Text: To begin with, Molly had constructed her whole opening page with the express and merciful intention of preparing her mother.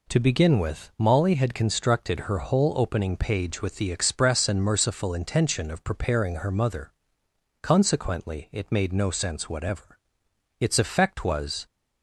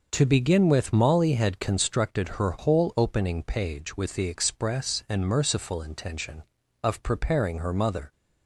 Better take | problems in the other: second | goes on to say "Consequently it made no sense whatever Its effect was"; strong; from 7.6 s on; 4.0 s long

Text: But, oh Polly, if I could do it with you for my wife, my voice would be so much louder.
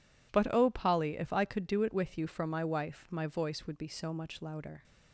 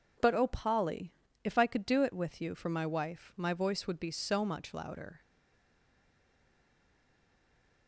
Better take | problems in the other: first | stays silent after the last word; strong; from 5.2 s on; 2.6 s long

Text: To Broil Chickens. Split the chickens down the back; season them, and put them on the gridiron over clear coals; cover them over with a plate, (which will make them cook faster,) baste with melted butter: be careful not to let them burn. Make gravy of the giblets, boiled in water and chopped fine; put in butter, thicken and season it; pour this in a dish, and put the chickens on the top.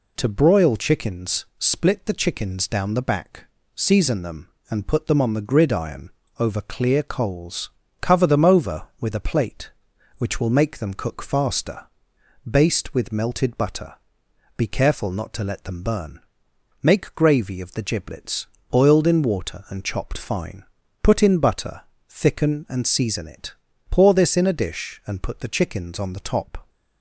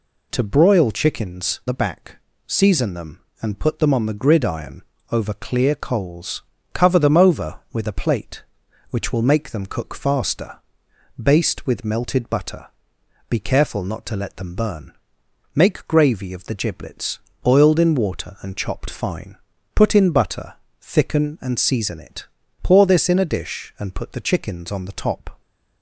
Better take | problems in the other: first | skips "Split the chickens down"; at 1.6 s // pauses between "gridiron" and "over"; slight; at 4.8 s; 0.28 s long; slight in the first

